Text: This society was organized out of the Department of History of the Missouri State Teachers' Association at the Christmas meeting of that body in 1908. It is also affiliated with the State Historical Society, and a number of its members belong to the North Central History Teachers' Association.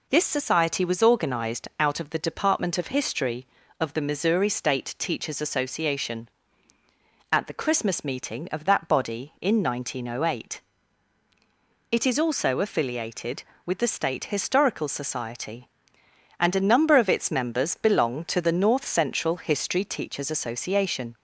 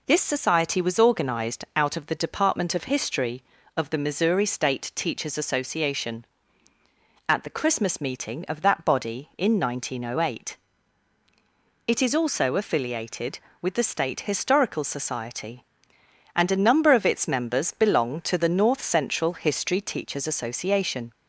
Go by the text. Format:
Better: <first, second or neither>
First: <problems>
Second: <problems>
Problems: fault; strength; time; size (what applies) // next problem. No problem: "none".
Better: neither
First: none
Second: none